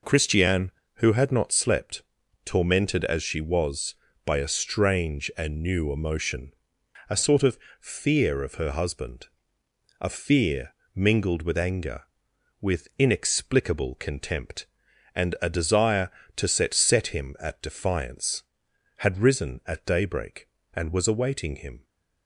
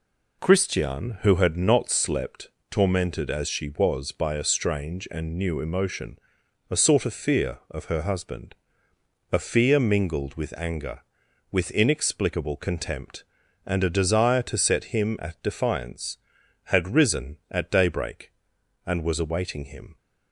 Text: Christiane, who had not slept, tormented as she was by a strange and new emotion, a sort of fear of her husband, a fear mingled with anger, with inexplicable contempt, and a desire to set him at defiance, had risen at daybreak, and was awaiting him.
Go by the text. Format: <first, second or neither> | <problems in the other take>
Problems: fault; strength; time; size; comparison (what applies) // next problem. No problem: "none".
second | pauses between "of" and "fear"; slight; at 7.5 s; 0.22 s long // pauses between "fear" and "mingled"; slight; at 10.7 s; 0.20 s long // says "set" twice; at 16.7 s